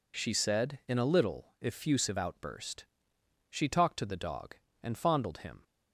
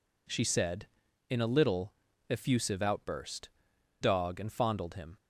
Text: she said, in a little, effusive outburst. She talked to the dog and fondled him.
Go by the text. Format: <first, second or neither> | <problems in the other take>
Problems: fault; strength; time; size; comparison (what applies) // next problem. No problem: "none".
first | skips "She talked to the"; at 3.7 s